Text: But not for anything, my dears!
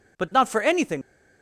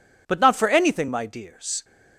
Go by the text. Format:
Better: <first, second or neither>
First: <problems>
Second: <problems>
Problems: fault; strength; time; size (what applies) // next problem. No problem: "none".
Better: second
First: stops before "my dears"; at 1.0 s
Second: none